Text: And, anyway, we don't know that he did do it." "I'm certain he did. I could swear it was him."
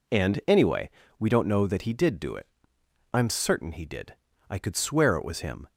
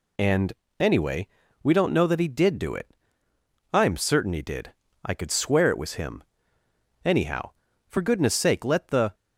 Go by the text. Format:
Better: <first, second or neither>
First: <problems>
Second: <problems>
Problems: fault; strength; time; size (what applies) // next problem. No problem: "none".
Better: first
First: none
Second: goes on to say "Anyhow for goodness sake let the"; strong; from 7.0 s on; 2.1 s long